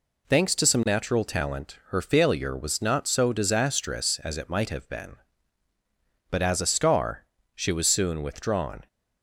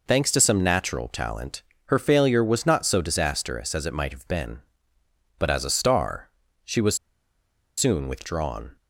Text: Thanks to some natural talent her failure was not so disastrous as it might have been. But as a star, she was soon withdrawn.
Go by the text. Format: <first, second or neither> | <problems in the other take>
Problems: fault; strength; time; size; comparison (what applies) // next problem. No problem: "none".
first | pauses between "talent" and "her"; slight; at 1.6 s; 0.24 s long // pauses between "was" and "soon"; noticeable; at 6.9 s; 0.81 s long